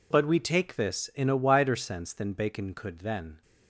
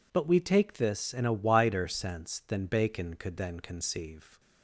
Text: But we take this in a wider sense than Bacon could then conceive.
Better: second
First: stops before "conceive"; at 3.4 s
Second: none

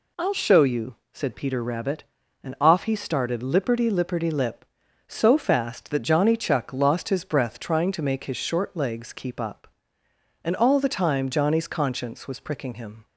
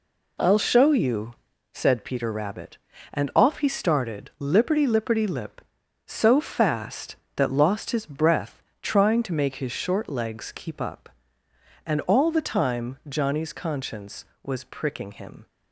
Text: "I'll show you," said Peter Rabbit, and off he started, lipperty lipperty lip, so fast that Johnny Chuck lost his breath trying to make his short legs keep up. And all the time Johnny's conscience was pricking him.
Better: first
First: none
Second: skips "Johnny Chuck"; at 7.4 s // pauses between "breath" and "trying"; slight; at 8.6 s; 0.22 s long

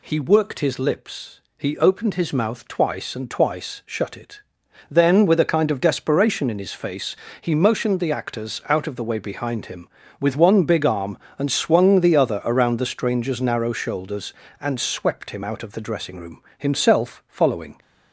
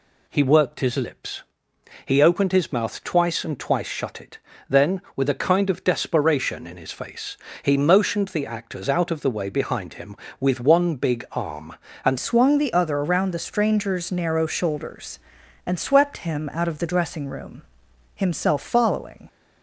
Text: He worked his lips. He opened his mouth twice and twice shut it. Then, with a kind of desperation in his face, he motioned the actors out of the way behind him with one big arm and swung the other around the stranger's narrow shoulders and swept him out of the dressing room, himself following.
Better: first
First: none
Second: changes voice at "swung"; from 12.1 s on; 7.1 s long

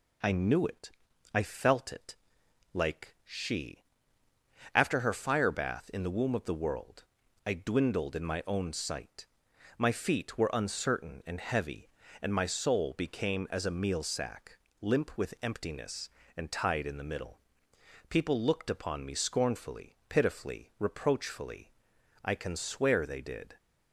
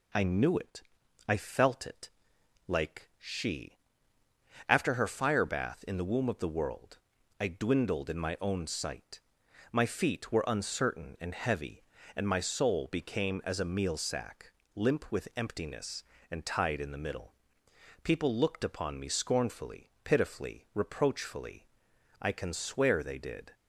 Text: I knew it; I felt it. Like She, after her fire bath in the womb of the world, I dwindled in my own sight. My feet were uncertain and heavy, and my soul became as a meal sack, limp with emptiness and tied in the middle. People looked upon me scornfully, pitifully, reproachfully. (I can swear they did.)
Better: neither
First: none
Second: none

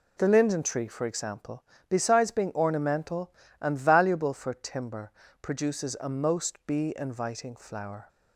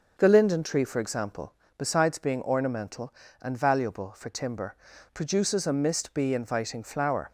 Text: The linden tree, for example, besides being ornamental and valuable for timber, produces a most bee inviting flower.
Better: first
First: none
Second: starts louder than the rest; until 1.1 s; 6 dB // says "mist" for "most"; at 5.7 s

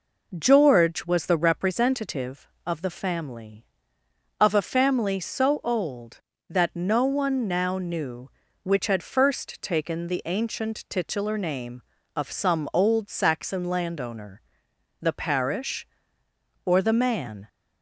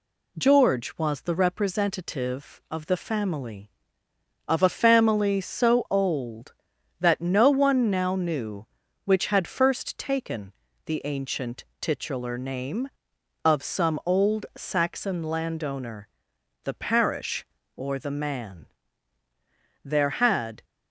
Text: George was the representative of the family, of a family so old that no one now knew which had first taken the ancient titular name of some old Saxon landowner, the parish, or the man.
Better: first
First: none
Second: pauses between "taken" and "the"; slight; at 10.5 s; 0.34 s long // pauses between "ancient" and "titular"; slight; at 11.6 s; 0.16 s long // goes on to say "There had"; noticeable; from 19.8 s on; 0.80 s long

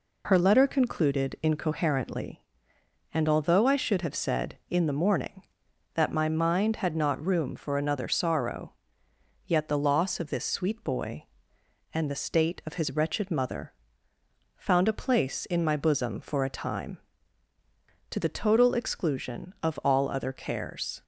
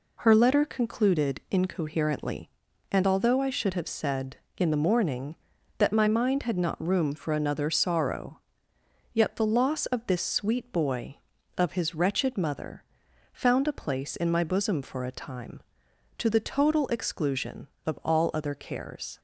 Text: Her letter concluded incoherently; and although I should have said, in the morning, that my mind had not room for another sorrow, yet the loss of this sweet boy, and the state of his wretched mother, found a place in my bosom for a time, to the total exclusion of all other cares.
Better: first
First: none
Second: skips "and the state"; at 11.3 s

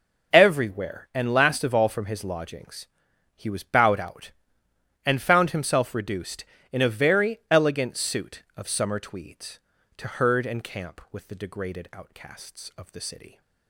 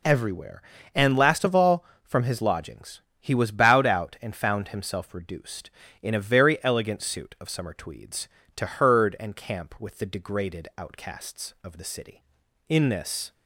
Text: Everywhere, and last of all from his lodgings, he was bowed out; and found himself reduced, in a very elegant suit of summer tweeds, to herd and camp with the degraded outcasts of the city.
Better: first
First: none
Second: goes on to say "In this"; noticeable; from 12.6 s on; 0.64 s long

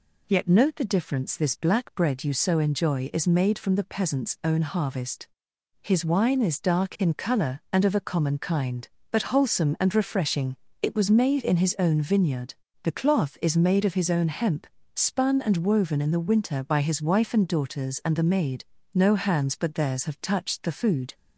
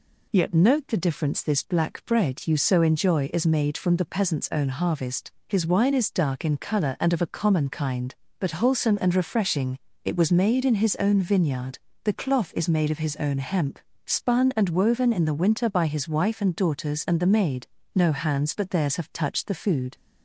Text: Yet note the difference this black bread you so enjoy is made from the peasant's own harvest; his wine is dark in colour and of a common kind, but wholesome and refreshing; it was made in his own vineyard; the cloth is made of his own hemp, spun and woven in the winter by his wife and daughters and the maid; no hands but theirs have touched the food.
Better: neither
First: none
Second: none

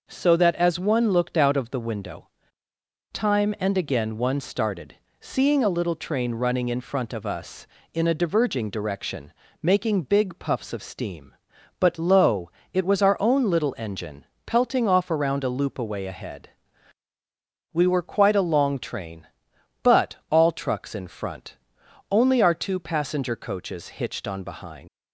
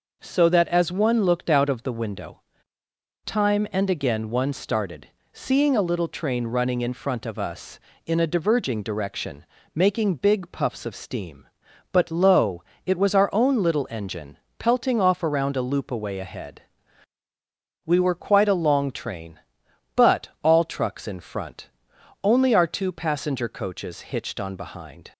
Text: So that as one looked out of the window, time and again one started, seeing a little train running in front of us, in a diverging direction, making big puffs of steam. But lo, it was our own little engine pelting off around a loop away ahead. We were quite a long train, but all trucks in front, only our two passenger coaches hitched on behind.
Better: second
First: pauses between "engine" and "pelting"; slight; at 14.2 s; 0.20 s long // pauses between "but" and "all"; slight; at 20.1 s; 0.16 s long // leaves "behind" unfinished; at 24.8 s; 115 ms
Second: pauses between "engine" and "pelting"; slight; at 14.3 s; 0.20 s long // pauses between "but" and "all"; slight; at 20.2 s; 0.16 s long

